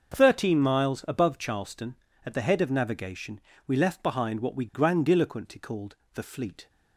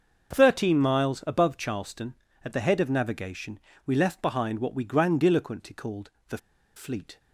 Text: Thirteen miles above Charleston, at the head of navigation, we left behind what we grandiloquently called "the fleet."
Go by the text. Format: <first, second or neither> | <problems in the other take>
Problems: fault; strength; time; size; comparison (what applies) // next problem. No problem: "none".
first | starts louder than the rest; until 1.4 s; 6.5 dB; also in the first // pauses between "called" and "the"; slight; at 6.0 s; 0.20 s long; slight in the first // pauses between "the" and "fleet"; at 6.3 s; 0.38 s long